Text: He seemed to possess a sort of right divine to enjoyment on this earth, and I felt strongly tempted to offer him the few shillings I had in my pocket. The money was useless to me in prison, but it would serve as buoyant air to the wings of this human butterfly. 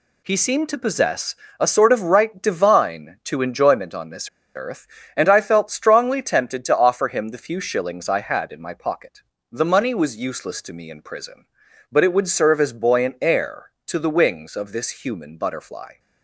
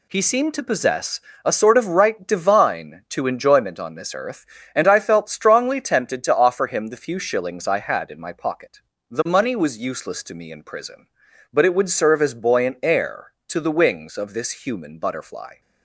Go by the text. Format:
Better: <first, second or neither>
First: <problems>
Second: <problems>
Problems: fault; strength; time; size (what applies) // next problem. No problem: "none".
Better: second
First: pauses between "possess" and "a"; slight; at 1.3 s; 0.24 s long // pauses between "this" and "earth"; slight; at 4.2 s; 0.26 s long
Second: pauses between "possess" and "a"; slight; at 1.1 s; 0.24 s long